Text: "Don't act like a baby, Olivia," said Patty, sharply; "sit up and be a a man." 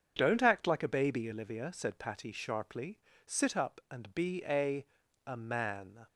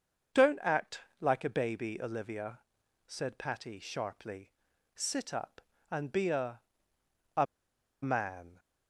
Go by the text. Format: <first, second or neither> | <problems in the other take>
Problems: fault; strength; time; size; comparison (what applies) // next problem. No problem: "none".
first | starts louder than the rest; until 1.5 s; 6.5 dB; strong in the first // pauses between "act" and "like"; slight; at 1.0 s; 0.20 s long // pauses between "a" and "a"; noticeable; at 6.6 s; 0.74 s long; also in the first // pauses between "a" and "man"; noticeable; at 7.4 s; 0.57 s long